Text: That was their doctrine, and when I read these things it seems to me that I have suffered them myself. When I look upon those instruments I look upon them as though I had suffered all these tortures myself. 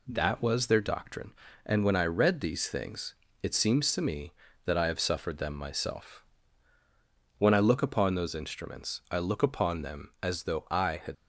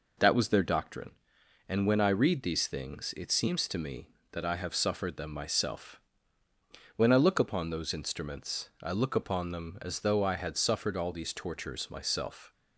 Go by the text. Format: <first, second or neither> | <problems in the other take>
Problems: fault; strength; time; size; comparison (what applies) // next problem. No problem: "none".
second | pauses between "things" and "it"; slight; at 3.1 s; 0.28 s long // stops before "suffered all these tortures myself"; at 11.1 s